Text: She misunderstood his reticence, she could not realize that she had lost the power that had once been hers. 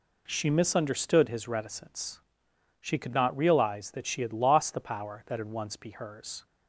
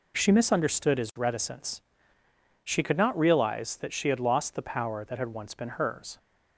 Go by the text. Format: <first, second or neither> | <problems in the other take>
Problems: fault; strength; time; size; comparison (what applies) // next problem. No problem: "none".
second | says "be" for "been"; at 5.7 s